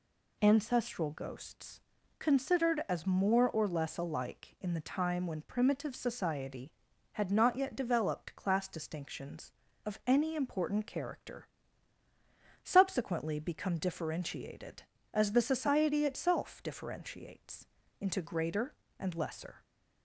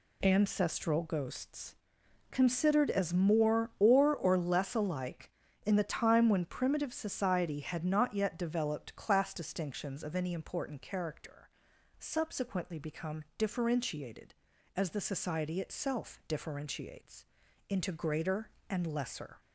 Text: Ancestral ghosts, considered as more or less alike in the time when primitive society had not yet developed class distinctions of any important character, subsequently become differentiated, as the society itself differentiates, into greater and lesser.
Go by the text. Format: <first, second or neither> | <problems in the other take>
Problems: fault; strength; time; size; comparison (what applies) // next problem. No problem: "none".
first | says "or" twice; at 4.1 s